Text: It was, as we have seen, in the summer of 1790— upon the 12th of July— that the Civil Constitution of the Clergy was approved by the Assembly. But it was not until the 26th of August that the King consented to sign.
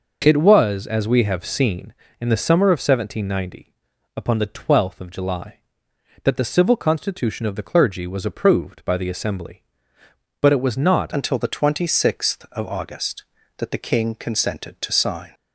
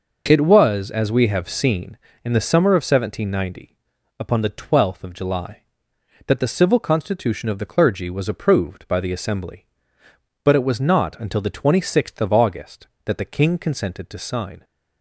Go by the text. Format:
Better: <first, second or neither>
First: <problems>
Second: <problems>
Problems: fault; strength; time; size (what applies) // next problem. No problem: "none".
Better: second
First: changes voice at "until"; from 11.1 s on; 4.2 s long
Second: none